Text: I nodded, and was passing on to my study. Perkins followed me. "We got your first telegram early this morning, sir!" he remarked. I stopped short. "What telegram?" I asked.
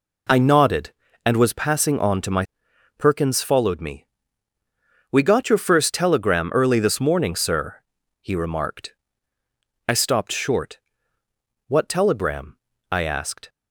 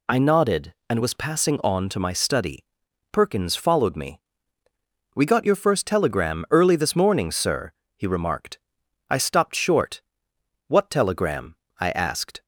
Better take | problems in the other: second | skips "study"; at 2.7 s

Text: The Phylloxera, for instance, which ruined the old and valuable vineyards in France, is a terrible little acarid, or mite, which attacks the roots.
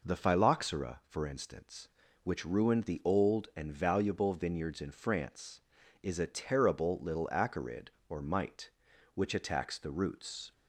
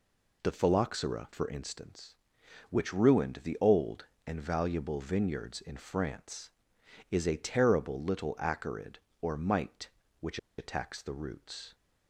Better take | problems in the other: first | pauses between "which" and "attacks"; slight; at 10.3 s; 0.20 s long

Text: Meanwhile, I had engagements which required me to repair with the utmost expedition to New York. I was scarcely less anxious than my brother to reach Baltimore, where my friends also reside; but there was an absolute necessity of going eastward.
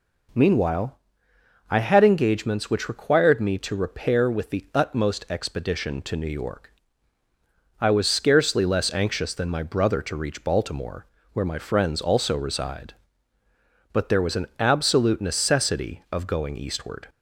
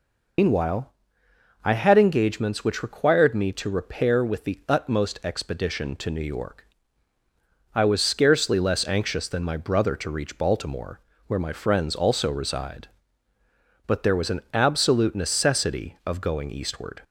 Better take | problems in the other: first | loses the start of "Meanwhile"; at 0.3 s; 145 ms

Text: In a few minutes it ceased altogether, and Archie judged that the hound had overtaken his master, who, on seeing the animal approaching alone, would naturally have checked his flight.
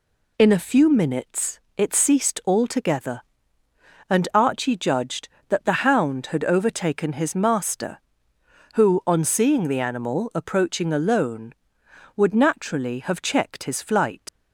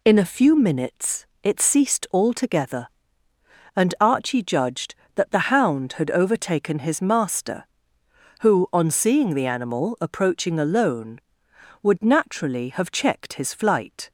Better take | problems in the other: second | pauses between "minutes" and "it"; slight; at 1.6 s; 0.16 s long; slight in the second // leaves "flight" unfinished; at 14.2 s; 95 ms

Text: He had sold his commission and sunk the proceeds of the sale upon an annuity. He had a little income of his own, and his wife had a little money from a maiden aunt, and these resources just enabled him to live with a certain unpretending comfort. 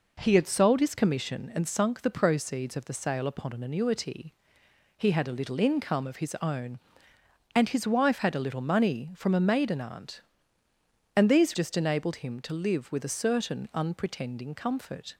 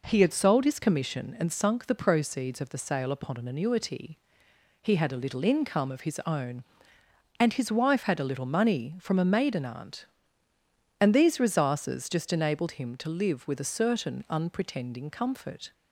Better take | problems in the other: second | skips "resources"; at 11.5 s

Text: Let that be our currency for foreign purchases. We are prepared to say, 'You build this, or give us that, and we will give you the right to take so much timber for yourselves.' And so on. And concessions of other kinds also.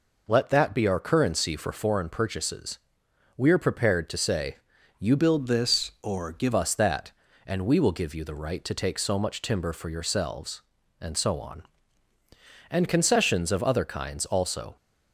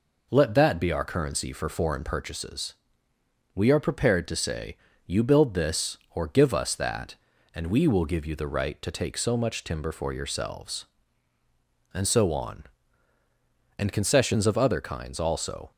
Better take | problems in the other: second | changes voice from "build" to "give"; from 5.1 to 6.5 s; 1.4 s long

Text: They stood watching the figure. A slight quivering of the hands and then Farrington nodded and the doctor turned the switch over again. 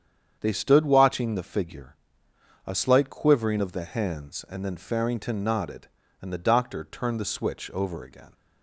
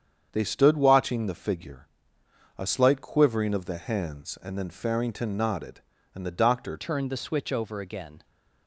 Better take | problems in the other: first | starts louder than the rest; strong; until 1.3 s; 8 dB; strong in the first // changes voice at "turned"; from 6.7 s on; 1.5 s long

